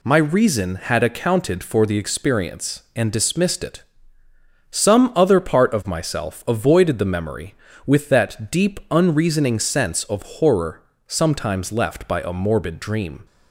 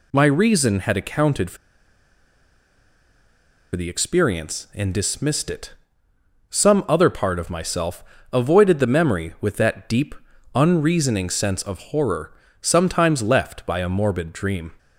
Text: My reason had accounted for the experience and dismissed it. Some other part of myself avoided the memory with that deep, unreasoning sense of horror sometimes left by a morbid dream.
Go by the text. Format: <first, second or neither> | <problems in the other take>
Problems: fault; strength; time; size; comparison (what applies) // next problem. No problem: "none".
first | pauses between "for" and "the"; strong; at 1.5 s; 2.1 s long // pauses between "myself" and "avoided"; slight; at 8.0 s; 0.28 s long // pauses between "horror" and "sometimes"; slight; at 12.3 s; 0.30 s long; slight in the first